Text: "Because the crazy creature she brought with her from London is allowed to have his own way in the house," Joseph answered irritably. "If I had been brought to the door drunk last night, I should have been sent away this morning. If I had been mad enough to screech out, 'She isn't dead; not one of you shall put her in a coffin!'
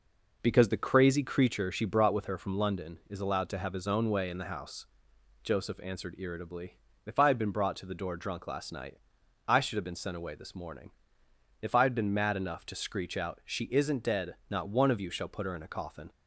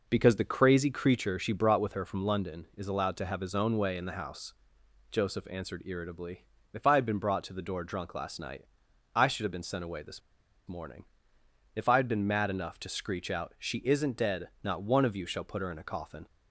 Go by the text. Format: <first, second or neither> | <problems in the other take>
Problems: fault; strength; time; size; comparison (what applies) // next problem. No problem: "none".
first | pauses between "this" and "morning"; noticeable; at 10.2 s; 0.46 s long